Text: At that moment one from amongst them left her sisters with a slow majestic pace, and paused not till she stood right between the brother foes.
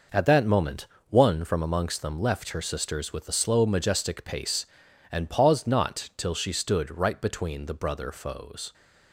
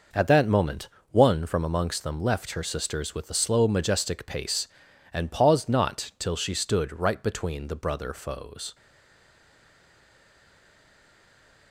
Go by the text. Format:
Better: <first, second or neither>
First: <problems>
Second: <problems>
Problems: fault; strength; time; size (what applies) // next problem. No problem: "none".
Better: first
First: pauses between "moment" and "one"; slight; at 0.8 s; 0.22 s long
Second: pauses between "moment" and "one"; slight; at 0.8 s; 0.22 s long // stays silent after the last word; strong; from 8.7 s on; 3.0 s long